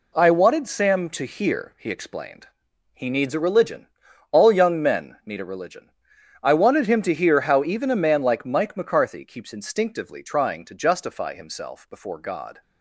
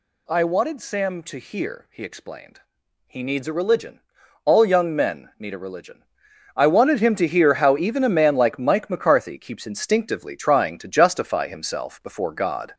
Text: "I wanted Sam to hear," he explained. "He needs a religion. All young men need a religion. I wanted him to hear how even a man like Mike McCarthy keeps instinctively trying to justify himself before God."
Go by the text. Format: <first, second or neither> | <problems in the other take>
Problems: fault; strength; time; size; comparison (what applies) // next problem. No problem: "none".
first | gets louder; slight; throughout; 3 dB